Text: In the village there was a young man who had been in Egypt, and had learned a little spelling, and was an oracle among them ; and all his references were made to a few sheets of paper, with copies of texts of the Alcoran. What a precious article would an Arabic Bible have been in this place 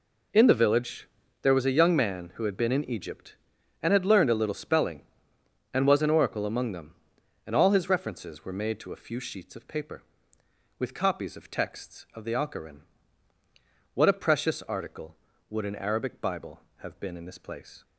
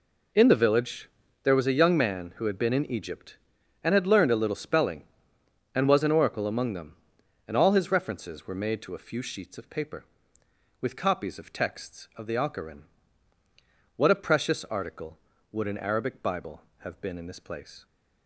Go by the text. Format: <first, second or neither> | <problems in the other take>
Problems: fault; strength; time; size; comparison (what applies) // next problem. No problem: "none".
neither | pauses between "village" and "there"; slight; the same in both